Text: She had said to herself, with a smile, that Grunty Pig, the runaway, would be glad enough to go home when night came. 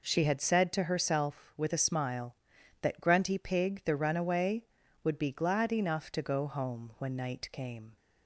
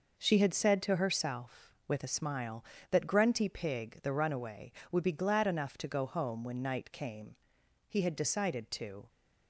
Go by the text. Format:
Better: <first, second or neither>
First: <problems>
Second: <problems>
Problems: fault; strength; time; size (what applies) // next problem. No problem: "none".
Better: first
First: none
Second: goes on to say "He had decided to"; noticeable; from 7.8 s on; 1.2 s long